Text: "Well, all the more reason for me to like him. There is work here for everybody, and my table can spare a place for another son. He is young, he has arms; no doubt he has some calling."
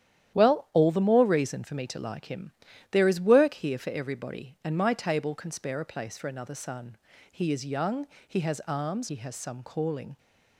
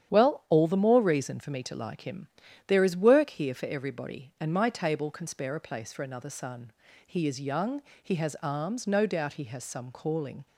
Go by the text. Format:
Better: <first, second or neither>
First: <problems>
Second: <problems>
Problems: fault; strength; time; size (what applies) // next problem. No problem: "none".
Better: second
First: starts louder than the rest; strong; until 1.3 s; 11 dB // skips "no doubt"; at 9.0 s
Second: starts louder than the rest; strong; until 1.1 s; 9.5 dB